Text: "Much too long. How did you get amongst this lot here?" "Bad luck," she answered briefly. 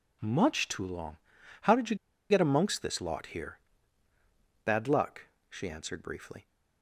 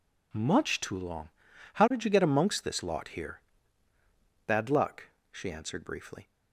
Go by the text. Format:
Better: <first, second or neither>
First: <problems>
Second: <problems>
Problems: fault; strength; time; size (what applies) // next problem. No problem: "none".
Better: second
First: pauses between "you" and "get"; slight; at 1.9 s; 0.35 s long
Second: none